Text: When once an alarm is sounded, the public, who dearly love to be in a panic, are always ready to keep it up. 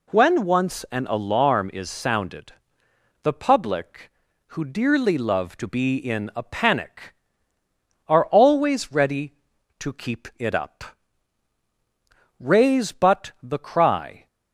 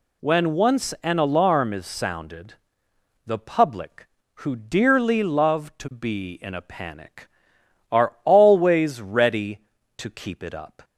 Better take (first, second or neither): second